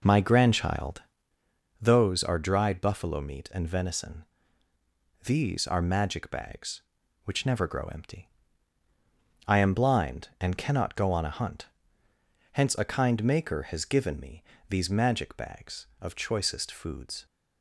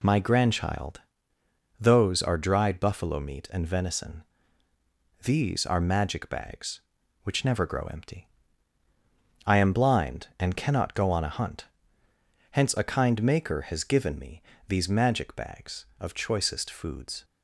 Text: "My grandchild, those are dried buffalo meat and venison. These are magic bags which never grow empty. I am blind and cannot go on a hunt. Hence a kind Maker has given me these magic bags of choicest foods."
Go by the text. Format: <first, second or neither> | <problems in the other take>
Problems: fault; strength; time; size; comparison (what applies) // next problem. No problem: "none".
second | starts louder than the rest; noticeable; until 1.4 s; 4.5 dB // pauses between "me" and "these"; slight; at 14.4 s; 0.24 s long; slight in the second